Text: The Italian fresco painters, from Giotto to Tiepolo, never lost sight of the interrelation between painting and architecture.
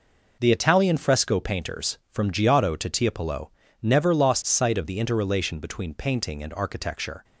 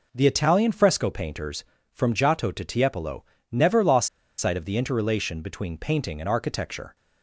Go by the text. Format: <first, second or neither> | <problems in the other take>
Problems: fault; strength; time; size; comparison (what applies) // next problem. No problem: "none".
first | pauses between "lost" and "sight"; slight; at 4.0 s; 0.30 s long